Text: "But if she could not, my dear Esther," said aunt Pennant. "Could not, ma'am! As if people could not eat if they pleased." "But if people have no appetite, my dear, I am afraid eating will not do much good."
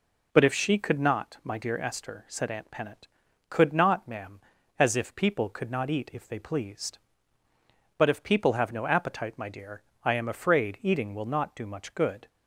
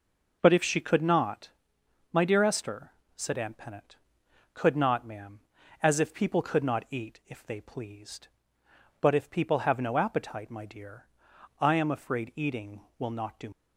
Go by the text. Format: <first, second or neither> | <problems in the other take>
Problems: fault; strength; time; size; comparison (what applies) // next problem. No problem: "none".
first | stops before "much good"; at 13.5 s